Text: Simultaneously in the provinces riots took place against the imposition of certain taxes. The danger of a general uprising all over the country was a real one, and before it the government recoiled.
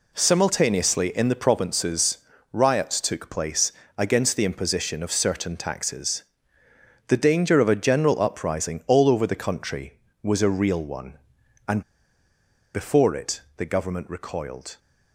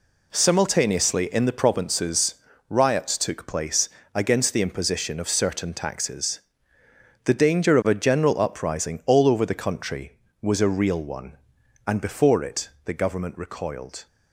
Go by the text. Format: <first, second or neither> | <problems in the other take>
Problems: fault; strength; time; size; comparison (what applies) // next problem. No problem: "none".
second | pauses between "provinces" and "riots"; slight; at 2.1 s; 0.34 s long; slight in the second // pauses between "place" and "against"; slight; at 3.7 s; 0.26 s long; slight in the second // pauses between "and" and "before"; noticeable; at 11.8 s; 0.93 s long // pauses between "it" and "the"; slight; at 13.4 s; 0.16 s long; slight in the second